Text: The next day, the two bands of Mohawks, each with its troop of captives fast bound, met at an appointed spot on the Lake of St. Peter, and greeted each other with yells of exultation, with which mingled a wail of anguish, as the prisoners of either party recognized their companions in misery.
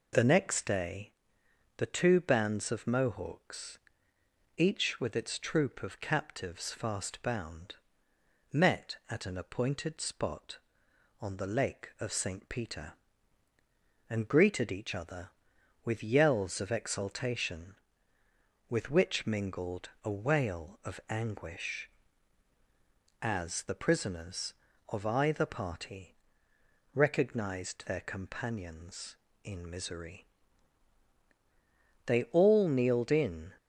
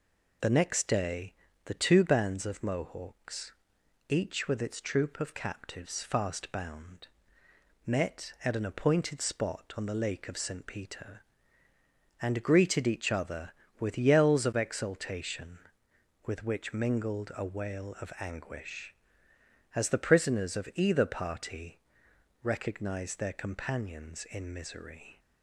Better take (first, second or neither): second